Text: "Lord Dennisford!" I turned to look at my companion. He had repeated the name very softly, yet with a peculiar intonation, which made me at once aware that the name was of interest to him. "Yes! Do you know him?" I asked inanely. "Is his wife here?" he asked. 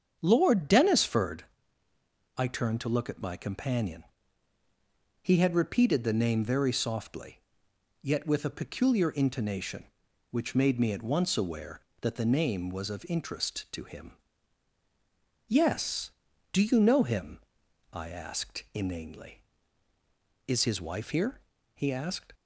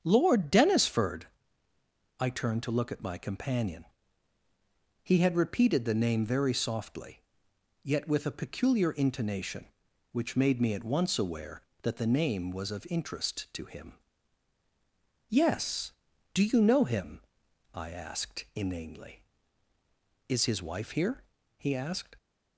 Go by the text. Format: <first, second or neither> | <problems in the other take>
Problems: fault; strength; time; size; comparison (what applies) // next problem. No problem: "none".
neither | starts louder than the rest; strong; the same in both